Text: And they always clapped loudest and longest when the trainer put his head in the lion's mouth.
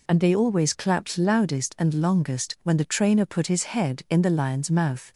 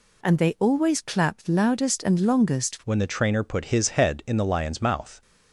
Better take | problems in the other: first | changes voice at "when"; from 2.8 s on; 2.4 s long

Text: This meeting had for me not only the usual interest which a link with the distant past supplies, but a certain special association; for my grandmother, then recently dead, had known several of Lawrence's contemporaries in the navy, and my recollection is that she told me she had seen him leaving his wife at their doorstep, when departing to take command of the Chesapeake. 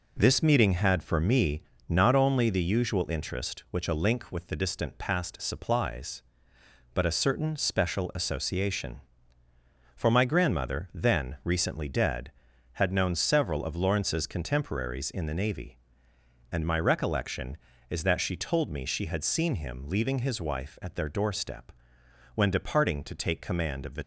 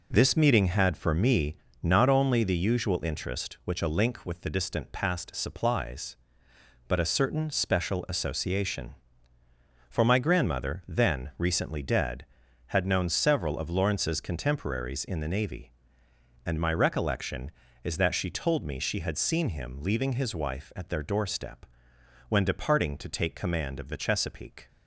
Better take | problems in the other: second | pauses between "me" and "not"; slight; at 1.6 s; 0.26 s long; slight in the second // stops before "Chesapeake"; at 24.0 s

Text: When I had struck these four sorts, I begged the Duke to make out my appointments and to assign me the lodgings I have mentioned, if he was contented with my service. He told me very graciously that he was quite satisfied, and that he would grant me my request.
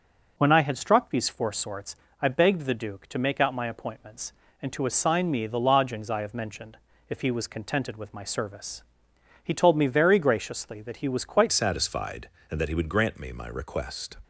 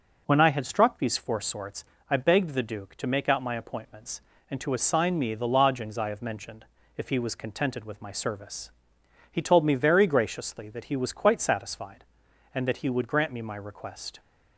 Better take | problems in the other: second | changes voice at "satisfied"; from 11.5 s on; 2.6 s long

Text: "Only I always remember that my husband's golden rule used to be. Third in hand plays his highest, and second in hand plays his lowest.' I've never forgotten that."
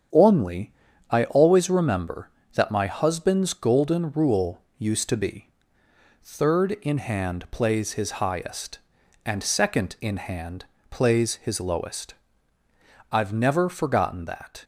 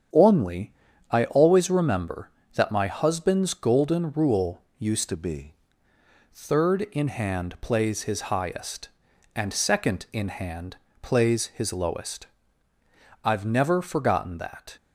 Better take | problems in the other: first | starts louder than the rest; strong; until 1.5 s; 7.5 dB; strong in the first // pauses between "Only" and "I"; slight; at 0.7 s; 0.36 s long; slight in the first // pauses between "rule" and "used"; slight; at 4.6 s; 0.16 s long; slight in the first // changes voice from "to" to "be"; from 5.0 to 5.5 s; 0.5 s long // pauses between "hand" and "plays"; slight; at 10.7 s; 0.24 s long; slight in the first

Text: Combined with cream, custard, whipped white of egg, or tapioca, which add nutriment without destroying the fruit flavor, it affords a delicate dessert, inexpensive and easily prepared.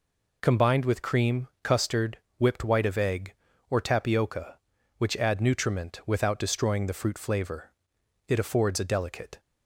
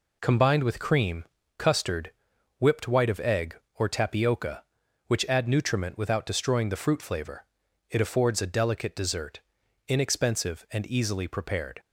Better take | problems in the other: second | stops before "dessert inexpensive and easily prepared"; at 9.3 s

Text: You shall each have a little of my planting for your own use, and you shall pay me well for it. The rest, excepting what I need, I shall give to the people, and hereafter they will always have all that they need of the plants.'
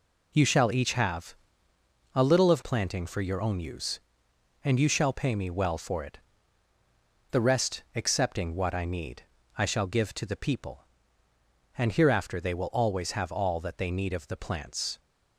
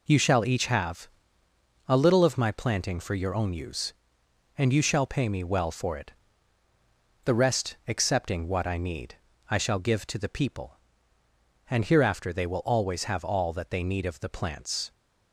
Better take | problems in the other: second | pauses between "have" and "a"; noticeable; at 1.3 s; 0.80 s long; noticeable in the second // skips "my"; at 2.6 s

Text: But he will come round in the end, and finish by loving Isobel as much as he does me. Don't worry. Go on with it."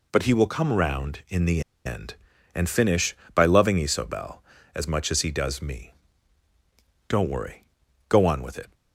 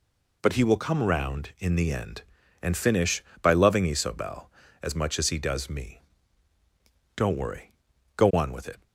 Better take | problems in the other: second | pauses between "the" and "end"; slight; at 1.6 s; 0.24 s long

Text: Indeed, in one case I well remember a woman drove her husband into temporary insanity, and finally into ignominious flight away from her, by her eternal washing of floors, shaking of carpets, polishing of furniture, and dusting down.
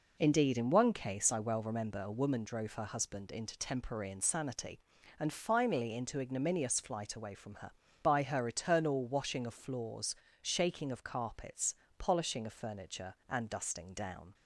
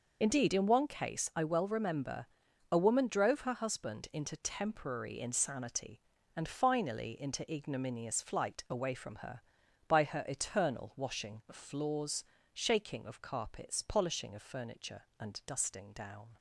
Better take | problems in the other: first | loses the start of "Indeed"; at 0.2 s; 40 ms // pauses between "remember" and "a"; at 2.2 s; 0.44 s long

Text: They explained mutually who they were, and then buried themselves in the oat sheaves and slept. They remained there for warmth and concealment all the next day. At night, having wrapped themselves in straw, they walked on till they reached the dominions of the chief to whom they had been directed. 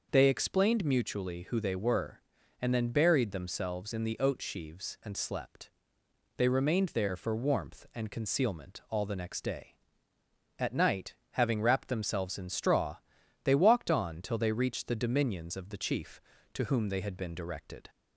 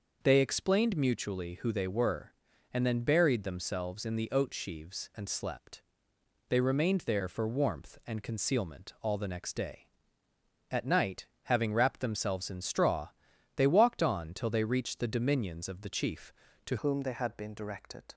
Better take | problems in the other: first | changes voice at "whom"; from 16.7 s on; 1.4 s long

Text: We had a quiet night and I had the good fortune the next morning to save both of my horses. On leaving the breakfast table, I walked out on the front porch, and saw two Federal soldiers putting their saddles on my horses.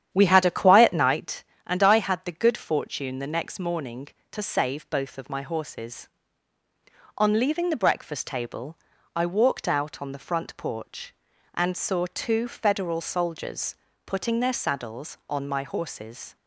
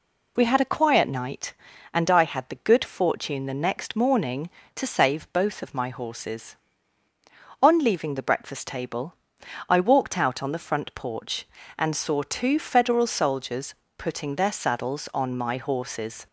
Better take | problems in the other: second | starts louder than the rest; strong; until 1.2 s; 10 dB // pauses between "soldiers" and "putting"; slight; at 13.7 s; 0.30 s long; slight in the second

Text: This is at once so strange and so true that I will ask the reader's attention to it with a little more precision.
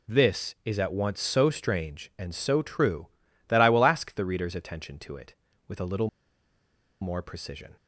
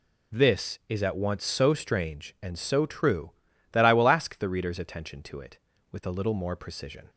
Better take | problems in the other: second | pauses between "little" and "more"; noticeable; at 6.0 s; 0.93 s long

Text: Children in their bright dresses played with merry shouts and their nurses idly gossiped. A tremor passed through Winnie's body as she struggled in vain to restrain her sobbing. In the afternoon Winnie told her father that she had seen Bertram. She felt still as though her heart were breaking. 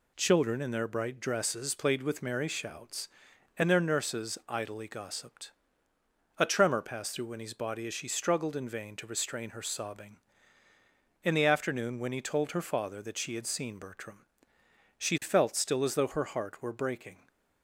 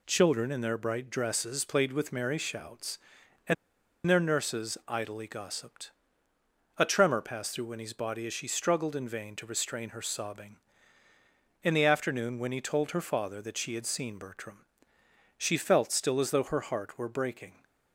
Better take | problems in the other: first | pauses between "and" and "their"; noticeable; at 3.5 s; 0.54 s long

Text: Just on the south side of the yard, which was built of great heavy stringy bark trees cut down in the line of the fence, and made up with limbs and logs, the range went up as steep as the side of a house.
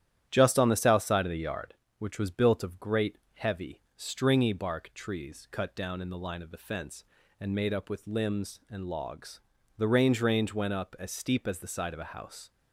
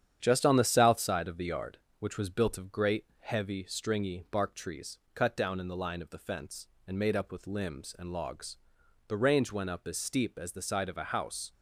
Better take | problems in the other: second | starts louder than the rest; strong; until 1.3 s; 11 dB; strong in the second // pauses between "great" and "heavy"; slight; at 3.1 s; 0.18 s long; slight in the second // pauses between "heavy" and "stringy"; slight; at 3.8 s; 0.16 s long // says "range" twice; at 10.2 s

